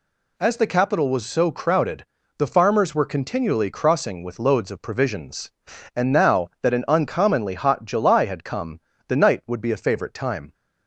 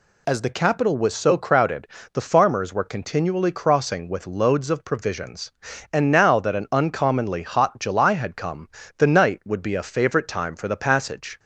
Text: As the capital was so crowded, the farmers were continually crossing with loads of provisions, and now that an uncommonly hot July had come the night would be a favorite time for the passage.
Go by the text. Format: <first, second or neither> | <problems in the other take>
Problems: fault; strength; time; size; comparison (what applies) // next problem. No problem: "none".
second | pauses between "come" and "the"; slight; at 8.8 s; 0.26 s long; slight in the second // stops before "for the passage"; at 10.5 s